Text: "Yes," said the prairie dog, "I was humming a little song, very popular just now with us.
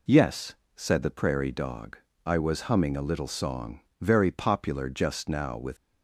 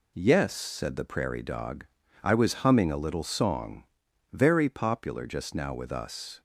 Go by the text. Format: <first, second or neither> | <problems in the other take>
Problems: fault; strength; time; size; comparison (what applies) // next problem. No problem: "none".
second | stops before "us"; at 5.7 s